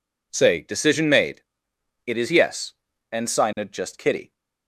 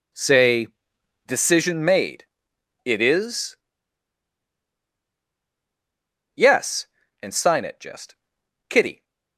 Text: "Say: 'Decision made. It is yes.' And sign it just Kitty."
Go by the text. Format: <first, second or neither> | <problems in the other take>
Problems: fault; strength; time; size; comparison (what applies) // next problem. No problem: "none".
first | pauses between "is" and "yes"; strong; at 3.5 s; 2.7 s long // pauses between "just" and "Kitty"; noticeable; at 8.1 s; 0.52 s long